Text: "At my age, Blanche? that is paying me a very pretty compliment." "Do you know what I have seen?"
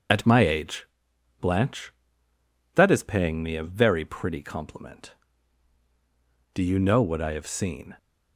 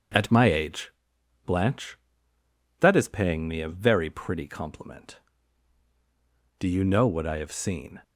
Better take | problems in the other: second | loses the start of "At"; at 0.0 s; 35 ms // starts louder than the rest; until 1.6 s; 6.5 dB; also in the second

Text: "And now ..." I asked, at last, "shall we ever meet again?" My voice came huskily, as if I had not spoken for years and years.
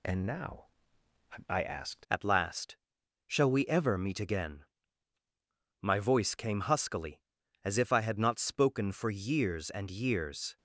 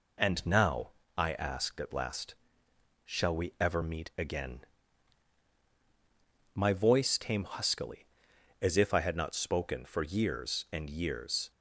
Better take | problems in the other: second | changes voice at "at"; from 2.1 s on; 8.4 s long

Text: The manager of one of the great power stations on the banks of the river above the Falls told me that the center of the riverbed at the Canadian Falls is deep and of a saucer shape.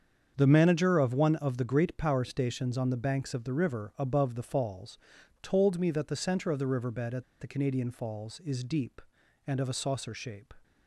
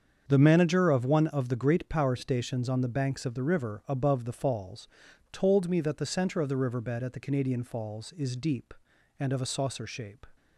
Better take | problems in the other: second | starts louder than the rest; strong; until 1.4 s; 7 dB; strong in the second // pauses between "Falls" and "told"; at 4.9 s; 0.44 s long; also in the second // pauses between "at" and "the"; slight; at 7.2 s; 0.16 s long

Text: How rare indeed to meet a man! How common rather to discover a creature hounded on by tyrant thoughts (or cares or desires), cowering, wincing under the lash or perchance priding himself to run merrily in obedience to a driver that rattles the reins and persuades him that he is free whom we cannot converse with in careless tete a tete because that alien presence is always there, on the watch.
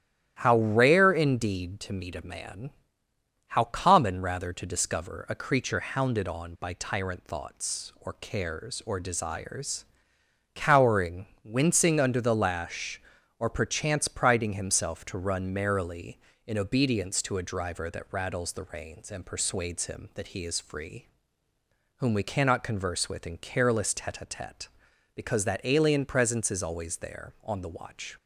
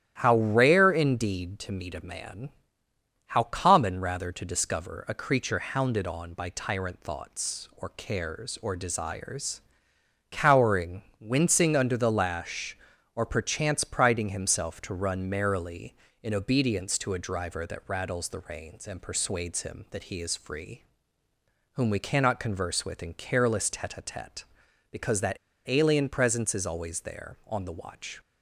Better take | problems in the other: first | starts louder than the rest; strong; until 1.2 s; 11.5 dB; strong in the first // pauses between "free" and "whom"; noticeable; at 20.8 s; 0.92 s long; noticeable in the first // pauses between "that" and "alien"; slight; at 25.3 s; 0.31 s long

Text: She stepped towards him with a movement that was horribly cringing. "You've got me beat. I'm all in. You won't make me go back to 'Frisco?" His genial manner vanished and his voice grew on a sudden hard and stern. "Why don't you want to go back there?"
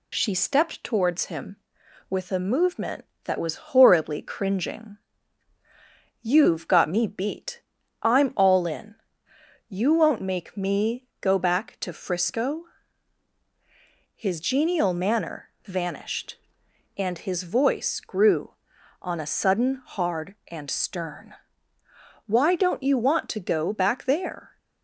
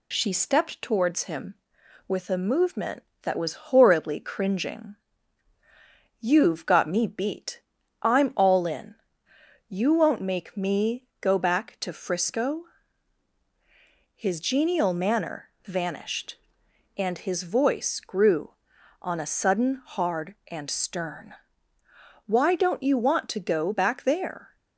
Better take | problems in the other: neither | pauses between "manner" and "vanished"; slight; the same in both

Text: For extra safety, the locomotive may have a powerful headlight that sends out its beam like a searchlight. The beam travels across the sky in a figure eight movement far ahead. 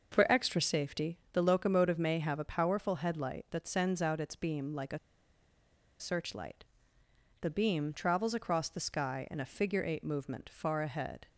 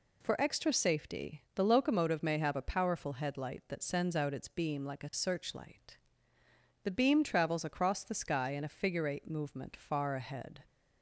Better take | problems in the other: second | starts louder than the rest; noticeable; until 1.1 s; 6 dB // pauses between "a" and "searchlight"; at 4.9 s; 1.0 s long

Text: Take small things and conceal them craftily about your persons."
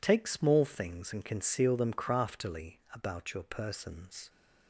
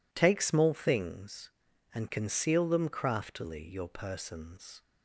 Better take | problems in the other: first | skips "about"; at 3.6 s

